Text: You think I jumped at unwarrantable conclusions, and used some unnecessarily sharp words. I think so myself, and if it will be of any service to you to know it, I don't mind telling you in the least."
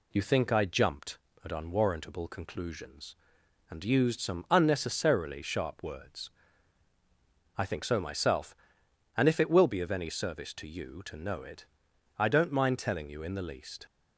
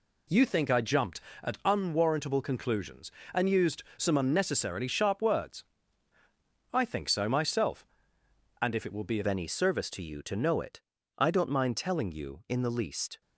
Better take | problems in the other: first | changes voice at "any"; from 9.2 s on; 4.0 s long

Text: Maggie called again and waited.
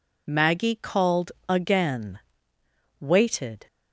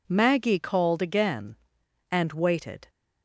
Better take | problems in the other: second | pauses between "called" and "again"; slight; at 1.3 s; 0.16 s long // skips "and"; at 2.5 s

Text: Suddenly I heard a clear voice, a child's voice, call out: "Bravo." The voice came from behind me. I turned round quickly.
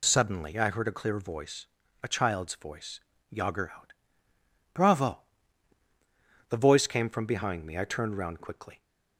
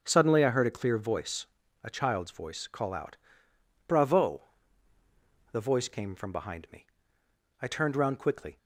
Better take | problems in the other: second | says "yager" for "call"; at 3.2 s

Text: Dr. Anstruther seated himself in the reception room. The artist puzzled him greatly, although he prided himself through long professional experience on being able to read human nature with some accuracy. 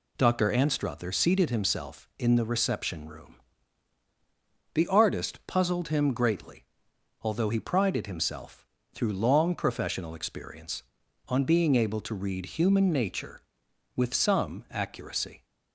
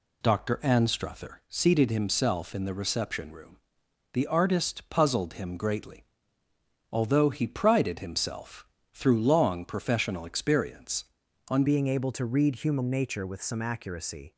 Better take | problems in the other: first | pauses between "himself" and "through"; slight; at 8.6 s; 0.30 s long; slight in the first // changes voice at "being"; from 11.6 s on; 2.7 s long

